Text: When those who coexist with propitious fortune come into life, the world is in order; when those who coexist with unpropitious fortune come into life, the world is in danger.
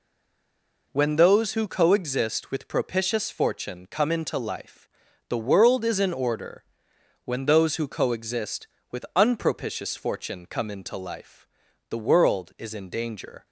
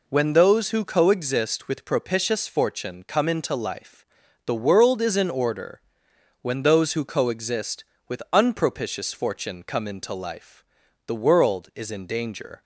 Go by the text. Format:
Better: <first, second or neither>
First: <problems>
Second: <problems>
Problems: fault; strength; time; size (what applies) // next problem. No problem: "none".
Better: second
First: stays silent before the first word; slight; until 0.9 s; 0.9 s long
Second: none